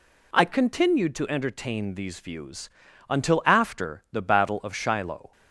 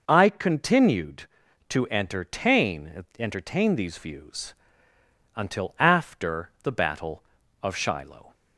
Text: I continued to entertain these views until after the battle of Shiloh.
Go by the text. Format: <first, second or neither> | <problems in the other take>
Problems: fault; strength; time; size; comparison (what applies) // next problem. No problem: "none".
first | says "entertain" twice; at 3.1 s // pauses between "views" and "until"; noticeable; at 4.5 s; 0.82 s long; also in the first